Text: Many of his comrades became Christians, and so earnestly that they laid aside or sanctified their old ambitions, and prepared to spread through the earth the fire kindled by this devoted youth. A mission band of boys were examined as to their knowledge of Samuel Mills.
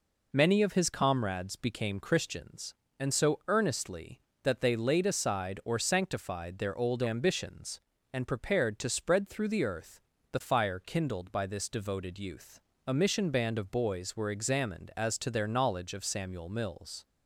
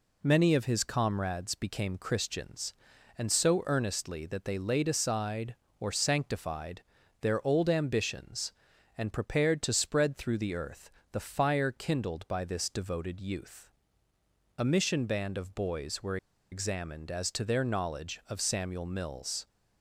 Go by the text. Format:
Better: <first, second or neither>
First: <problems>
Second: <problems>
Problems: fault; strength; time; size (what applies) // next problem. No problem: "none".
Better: first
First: pauses between "earth" and "the"; slight; at 9.9 s; 0.32 s long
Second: pauses between "sanctified" and "their"; at 6.8 s; 0.40 s long // pauses between "earth" and "the"; slight; at 10.9 s; 0.22 s long // pauses between "were" and "examined"; slight; at 16.1 s; 0.34 s long